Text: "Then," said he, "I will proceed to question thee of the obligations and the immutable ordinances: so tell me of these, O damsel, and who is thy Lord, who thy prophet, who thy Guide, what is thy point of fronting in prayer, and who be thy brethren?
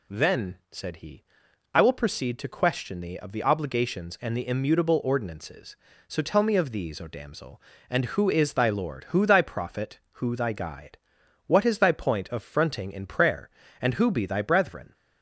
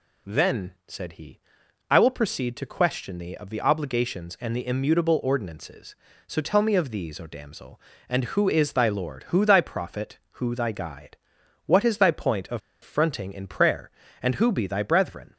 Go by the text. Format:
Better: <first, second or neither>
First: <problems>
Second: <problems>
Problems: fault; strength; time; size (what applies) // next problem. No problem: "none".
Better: first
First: none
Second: pauses between "of" and "fronting"; slight; at 12.6 s; 0.23 s long